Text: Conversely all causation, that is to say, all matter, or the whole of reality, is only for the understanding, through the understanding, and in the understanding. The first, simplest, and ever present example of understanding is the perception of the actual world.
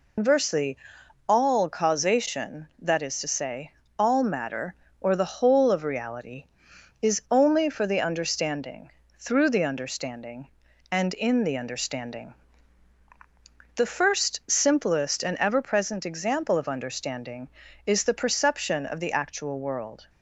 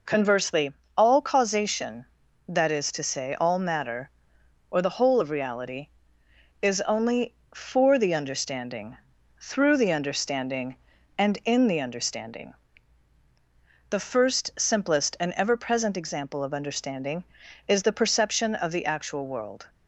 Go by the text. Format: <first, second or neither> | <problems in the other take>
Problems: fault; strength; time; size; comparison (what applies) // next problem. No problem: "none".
second | loses the start of "Conversely"; at 0.1 s; 140 ms // pauses between "Conversely" and "all"; noticeable; at 0.7 s; 0.50 s long; slight in the second